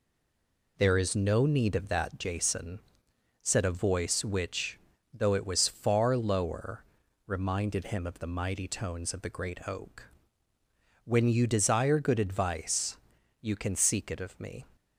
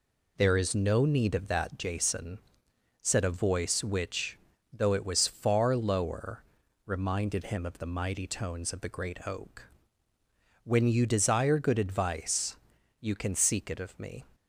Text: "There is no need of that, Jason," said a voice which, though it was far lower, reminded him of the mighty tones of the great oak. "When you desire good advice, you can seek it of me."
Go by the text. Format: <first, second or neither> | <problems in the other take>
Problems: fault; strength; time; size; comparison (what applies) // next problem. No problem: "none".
second | stays silent before the first word; slight; until 0.7 s; 0.7 s long